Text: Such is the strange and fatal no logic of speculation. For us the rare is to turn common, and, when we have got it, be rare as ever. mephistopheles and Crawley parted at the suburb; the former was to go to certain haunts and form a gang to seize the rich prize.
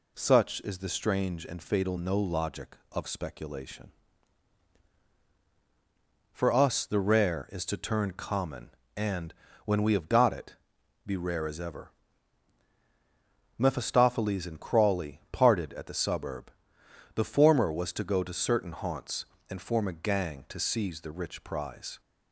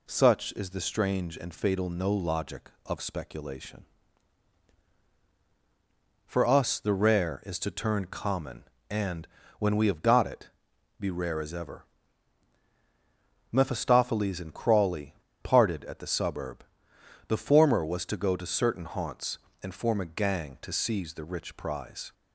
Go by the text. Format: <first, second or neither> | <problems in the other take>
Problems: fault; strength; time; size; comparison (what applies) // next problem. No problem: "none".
first | pauses between "Crawley" and "parted"; slight; at 15.1 s; 0.29 s long